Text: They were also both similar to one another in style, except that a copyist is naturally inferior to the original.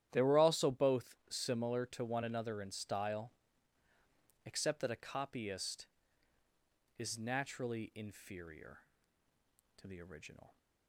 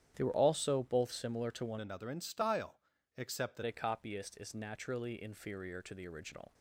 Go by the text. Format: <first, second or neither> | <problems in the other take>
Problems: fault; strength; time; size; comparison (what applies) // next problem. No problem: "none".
first | starts louder than the rest; strong; until 1.1 s; 10.5 dB; strong in the first // changes voice from "another" to "that"; from 1.7 to 3.6 s; 1.9 s long